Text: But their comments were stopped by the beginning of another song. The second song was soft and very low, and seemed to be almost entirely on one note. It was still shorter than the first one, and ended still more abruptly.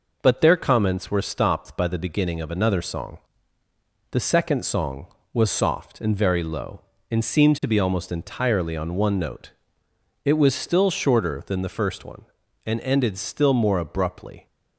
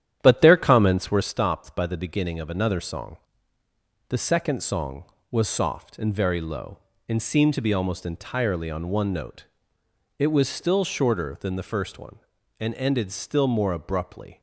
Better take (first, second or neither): first